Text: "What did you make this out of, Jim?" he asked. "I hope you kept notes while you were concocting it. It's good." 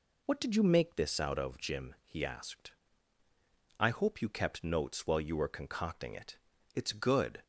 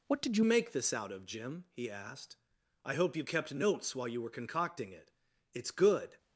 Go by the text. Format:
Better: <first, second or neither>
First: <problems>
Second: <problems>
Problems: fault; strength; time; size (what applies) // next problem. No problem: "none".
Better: first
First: none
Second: changes voice at "make"; from 0.4 s on; 5.7 s long